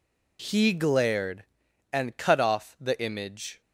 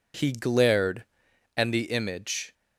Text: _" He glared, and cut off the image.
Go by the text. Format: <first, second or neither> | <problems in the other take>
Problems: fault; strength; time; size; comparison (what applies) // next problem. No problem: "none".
first | skips "cut off"; at 1.7 s